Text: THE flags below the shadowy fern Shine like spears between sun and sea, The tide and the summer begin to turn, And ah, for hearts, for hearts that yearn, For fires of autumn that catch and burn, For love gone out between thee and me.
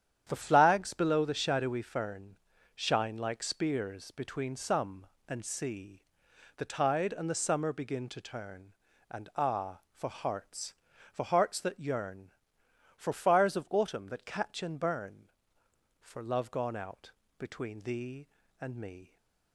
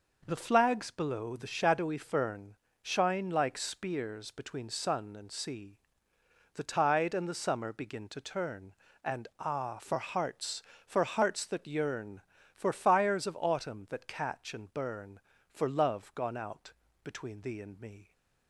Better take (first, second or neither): second